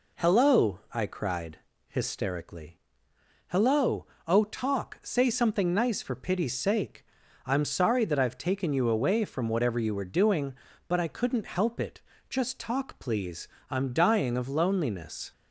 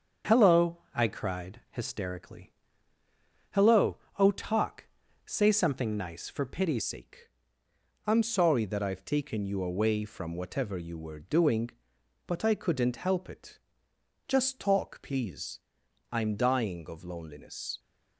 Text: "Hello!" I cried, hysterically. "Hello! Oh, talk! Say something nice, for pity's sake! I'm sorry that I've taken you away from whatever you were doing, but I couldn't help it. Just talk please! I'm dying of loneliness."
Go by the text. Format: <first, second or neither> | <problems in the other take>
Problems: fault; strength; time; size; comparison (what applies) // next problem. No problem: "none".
first | starts louder than the rest; until 1.4 s; 7 dB // changes voice at "sake"; from 6.8 s on; 10.9 s long